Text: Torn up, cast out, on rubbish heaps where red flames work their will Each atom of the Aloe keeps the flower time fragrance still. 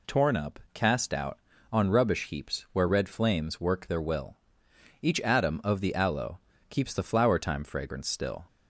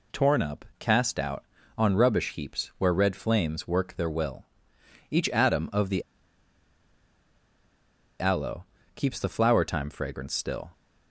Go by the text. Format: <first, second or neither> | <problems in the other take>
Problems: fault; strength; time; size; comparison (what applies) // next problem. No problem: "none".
first | pauses between "will" and "Each"; noticeable; at 4.4 s; 0.64 s long; noticeable in the first // pauses between "the" and "Aloe"; strong; at 6.0 s; 2.1 s long // pauses between "Aloe" and "keeps"; slight; at 8.6 s; 0.30 s long; slight in the first